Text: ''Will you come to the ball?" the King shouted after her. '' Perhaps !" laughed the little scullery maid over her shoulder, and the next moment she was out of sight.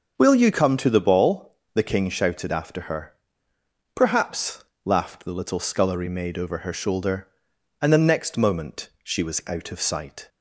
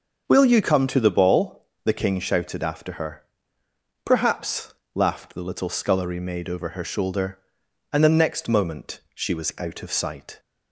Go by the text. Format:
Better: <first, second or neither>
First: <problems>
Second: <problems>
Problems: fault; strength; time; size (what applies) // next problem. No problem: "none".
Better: neither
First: none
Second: none